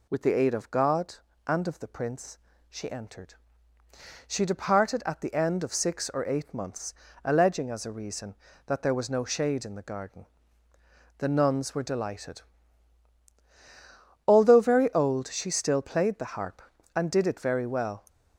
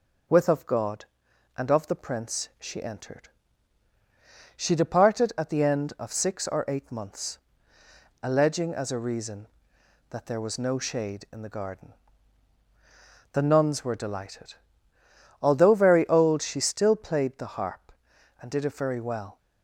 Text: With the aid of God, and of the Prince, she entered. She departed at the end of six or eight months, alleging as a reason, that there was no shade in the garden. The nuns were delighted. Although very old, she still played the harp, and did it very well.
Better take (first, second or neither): first